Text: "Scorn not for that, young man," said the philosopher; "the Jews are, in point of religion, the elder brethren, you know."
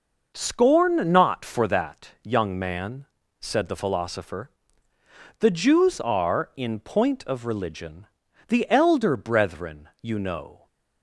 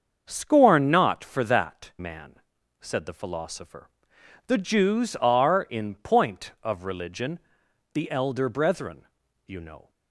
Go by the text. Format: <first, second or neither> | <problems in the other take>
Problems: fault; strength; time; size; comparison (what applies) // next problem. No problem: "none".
first | starts louder than the rest; until 1.2 s; 6.5 dB // skips "young"; at 1.9 s